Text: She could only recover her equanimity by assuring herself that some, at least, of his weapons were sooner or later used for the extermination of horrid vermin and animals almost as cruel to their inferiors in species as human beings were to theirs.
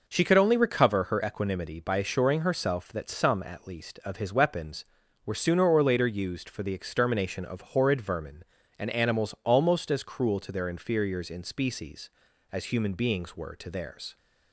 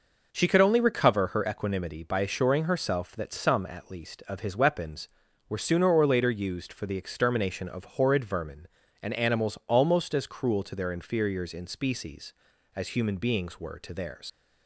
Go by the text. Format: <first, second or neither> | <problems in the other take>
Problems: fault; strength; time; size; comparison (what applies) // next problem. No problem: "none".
first | leaves "theirs" unfinished; at 14.2 s; 95 ms